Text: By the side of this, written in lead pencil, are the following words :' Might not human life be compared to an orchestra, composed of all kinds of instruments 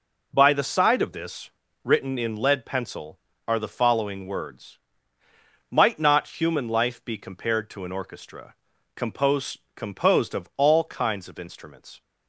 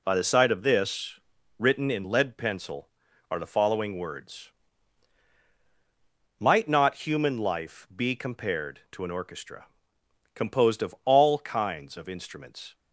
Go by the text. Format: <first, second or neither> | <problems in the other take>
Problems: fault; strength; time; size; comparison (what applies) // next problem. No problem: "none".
second | says "composed" twice; at 9.7 s